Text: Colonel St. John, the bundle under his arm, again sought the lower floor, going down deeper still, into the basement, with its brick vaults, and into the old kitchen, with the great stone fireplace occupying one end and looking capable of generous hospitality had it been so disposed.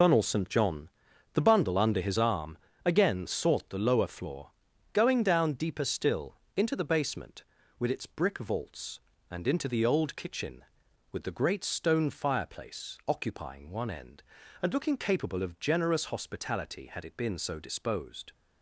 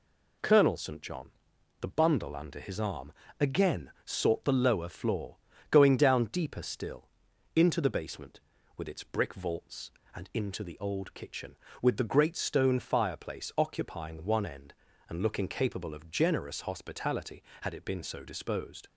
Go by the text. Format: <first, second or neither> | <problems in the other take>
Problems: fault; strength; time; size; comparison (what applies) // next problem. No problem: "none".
second | loses the start of "Colonel"; at 0.0 s; 105 ms